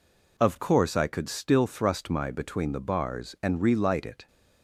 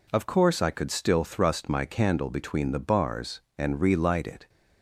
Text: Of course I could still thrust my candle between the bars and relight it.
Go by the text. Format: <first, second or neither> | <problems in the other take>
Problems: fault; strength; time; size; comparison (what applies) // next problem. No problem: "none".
second | skips "candle"; at 2.2 s